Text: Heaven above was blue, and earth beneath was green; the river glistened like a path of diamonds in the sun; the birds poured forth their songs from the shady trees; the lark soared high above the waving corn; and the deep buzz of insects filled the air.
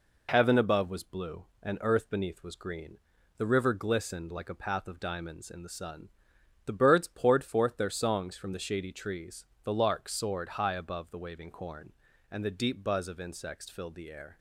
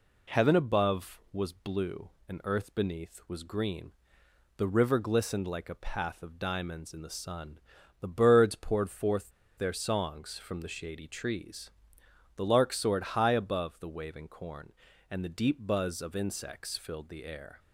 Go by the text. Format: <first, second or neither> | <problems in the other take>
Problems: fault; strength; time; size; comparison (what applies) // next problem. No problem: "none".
first | pauses between "forth" and "their"; slight; at 9.3 s; 0.27 s long